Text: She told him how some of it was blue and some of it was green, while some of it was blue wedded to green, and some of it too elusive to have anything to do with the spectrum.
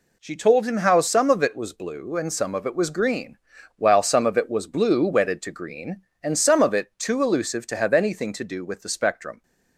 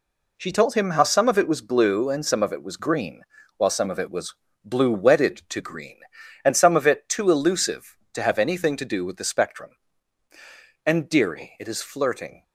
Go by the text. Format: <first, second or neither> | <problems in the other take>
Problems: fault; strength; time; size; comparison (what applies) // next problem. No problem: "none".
first | pauses between "was" and "blue"; slight; at 4.3 s; 0.28 s long // goes on to say "And dearie it is flirting"; from 10.8 s on; 1.5 s long